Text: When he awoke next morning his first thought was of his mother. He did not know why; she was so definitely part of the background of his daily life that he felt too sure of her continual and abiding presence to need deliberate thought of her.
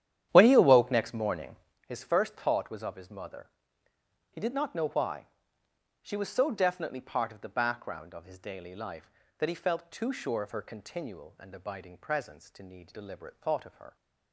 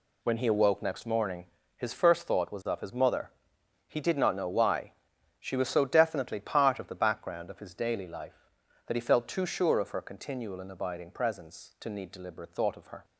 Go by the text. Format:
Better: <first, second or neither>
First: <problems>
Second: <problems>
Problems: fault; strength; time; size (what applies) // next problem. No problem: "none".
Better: second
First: starts louder than the rest; strong; until 1.9 s; 10.5 dB // pauses between "morning" and "his"; slight; at 1.5 s; 0.32 s long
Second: pauses between "morning" and "his"; slight; at 1.4 s; 0.30 s long